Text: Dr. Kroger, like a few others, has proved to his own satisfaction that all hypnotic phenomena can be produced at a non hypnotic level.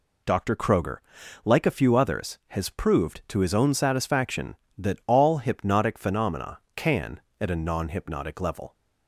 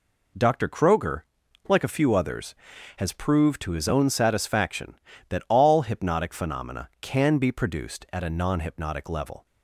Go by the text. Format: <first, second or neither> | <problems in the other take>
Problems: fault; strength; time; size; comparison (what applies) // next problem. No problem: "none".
second | skips "be produced"; at 7.2 s